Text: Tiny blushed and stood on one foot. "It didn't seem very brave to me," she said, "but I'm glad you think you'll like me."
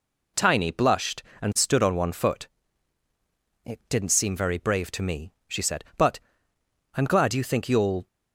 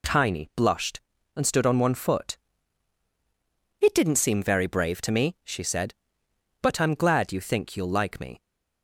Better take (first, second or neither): second